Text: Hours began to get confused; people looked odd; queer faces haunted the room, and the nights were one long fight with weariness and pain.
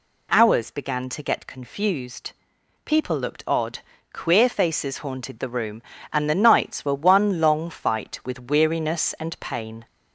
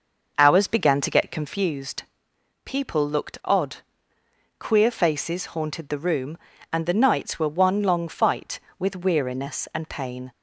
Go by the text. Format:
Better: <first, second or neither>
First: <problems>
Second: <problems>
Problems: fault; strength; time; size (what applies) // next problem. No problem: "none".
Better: first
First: none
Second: starts louder than the rest; noticeable; until 1.7 s; 6 dB